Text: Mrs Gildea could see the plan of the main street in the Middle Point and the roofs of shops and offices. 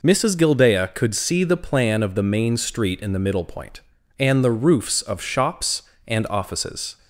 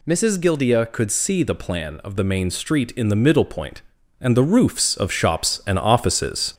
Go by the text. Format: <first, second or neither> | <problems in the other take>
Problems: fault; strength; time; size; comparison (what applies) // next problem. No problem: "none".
first | gets louder; throughout; 3.5 dB